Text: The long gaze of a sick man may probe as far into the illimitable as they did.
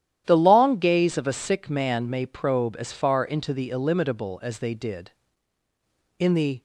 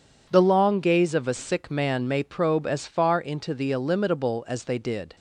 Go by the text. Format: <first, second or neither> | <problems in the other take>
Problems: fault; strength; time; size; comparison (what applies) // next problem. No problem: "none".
second | starts louder than the rest; strong; until 1.2 s; 11.5 dB // goes on to say "In the"; slight; from 6.1 s on; 0.44 s long